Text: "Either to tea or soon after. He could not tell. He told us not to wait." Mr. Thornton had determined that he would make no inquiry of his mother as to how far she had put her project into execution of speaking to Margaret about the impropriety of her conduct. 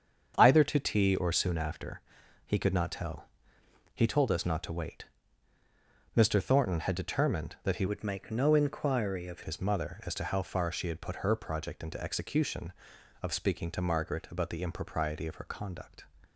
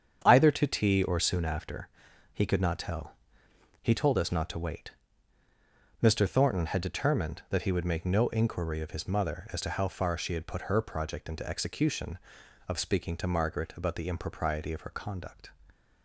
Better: second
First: starts louder than the rest; strong; until 1.3 s; 7 dB // changes voice from "would" to "of"; from 7.8 to 9.4 s; 1.6 s long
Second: starts louder than the rest; strong; until 1.2 s; 8 dB

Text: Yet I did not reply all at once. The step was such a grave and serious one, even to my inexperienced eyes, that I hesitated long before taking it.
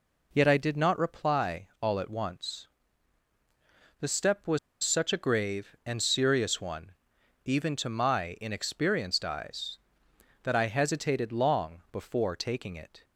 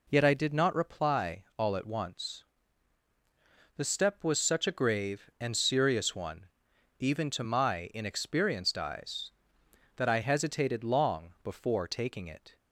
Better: second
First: pauses between "was" and "such"; slight; at 4.5 s; 0.25 s long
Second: none

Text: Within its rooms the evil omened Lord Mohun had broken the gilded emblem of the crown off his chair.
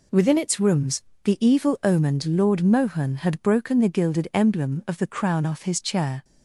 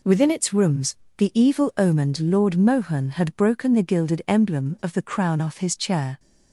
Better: neither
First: pauses between "rooms" and "the"; slight; at 1.0 s; 0.22 s long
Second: pauses between "rooms" and "the"; slight; at 0.9 s; 0.22 s long

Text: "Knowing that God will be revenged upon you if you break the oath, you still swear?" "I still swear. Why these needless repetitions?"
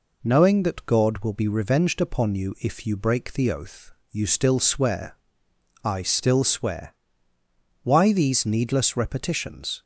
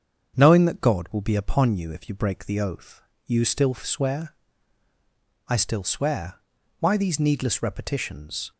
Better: first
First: none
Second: starts louder than the rest; strong; until 1.4 s; 7.5 dB // skips "revenged"; at 1.3 s

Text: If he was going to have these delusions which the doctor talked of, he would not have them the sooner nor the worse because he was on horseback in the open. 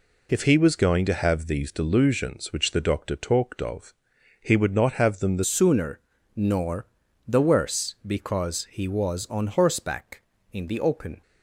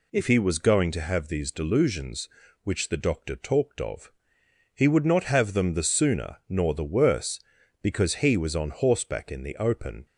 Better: second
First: changes voice at "sooner"; from 5.4 s on; 5.8 s long // pauses between "sooner" and "nor"; slight; at 5.9 s; 0.36 s long // pauses between "nor" and "the"; at 6.8 s; 0.42 s long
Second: none

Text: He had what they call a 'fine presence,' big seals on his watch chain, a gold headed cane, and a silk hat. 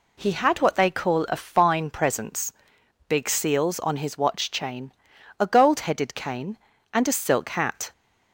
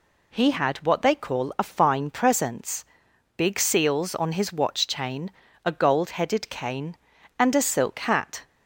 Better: neither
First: none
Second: none

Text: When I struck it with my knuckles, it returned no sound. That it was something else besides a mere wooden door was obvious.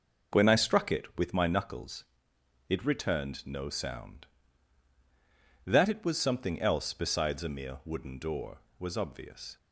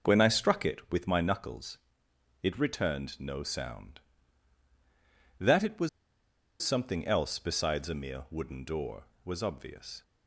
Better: first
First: none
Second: pauses between "was" and "something"; noticeable; at 5.8 s; 0.73 s long

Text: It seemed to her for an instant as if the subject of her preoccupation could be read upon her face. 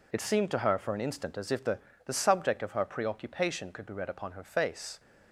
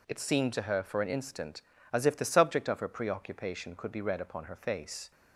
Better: second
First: says "the" twice; at 2.0 s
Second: none

